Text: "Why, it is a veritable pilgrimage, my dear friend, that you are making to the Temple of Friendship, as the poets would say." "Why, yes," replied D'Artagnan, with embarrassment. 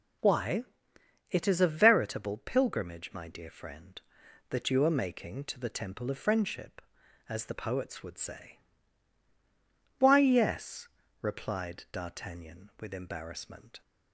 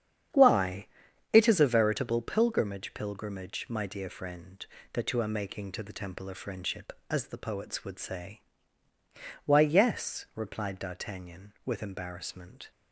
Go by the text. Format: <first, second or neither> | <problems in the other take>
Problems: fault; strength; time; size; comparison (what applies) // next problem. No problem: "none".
first | starts louder than the rest; strong; until 1.7 s; 9 dB // says "pilgrimage" twice; at 2.9 s